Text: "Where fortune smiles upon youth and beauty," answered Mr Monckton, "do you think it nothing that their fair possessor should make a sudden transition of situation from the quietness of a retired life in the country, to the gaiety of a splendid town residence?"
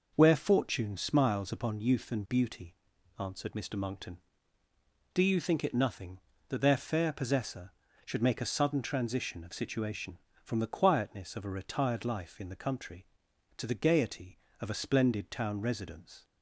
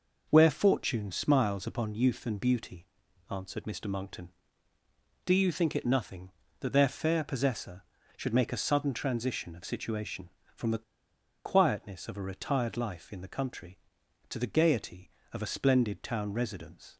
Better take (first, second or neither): first